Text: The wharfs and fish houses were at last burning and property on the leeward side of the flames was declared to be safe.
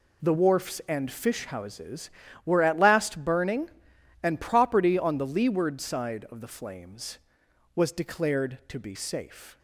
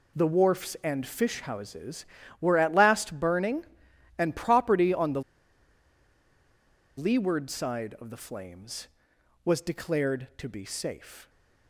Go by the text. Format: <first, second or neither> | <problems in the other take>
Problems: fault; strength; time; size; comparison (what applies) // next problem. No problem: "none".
first | pauses between "the" and "leeward"; strong; at 5.2 s; 1.7 s long